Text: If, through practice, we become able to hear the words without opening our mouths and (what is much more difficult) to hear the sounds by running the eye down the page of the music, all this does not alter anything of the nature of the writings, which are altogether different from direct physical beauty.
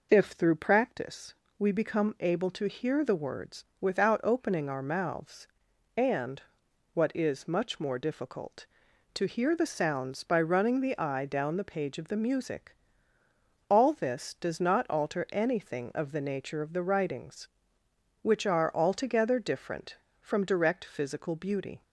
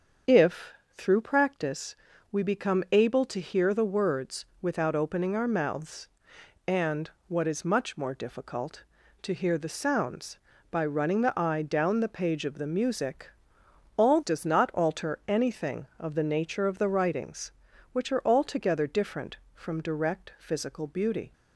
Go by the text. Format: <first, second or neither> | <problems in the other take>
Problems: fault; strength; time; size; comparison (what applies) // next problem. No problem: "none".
first | starts louder than the rest; until 1.4 s; 7 dB // pauses between "words" and "without"; slight; at 4.4 s; 0.16 s long; slight in the first // skips "this"; at 14.2 s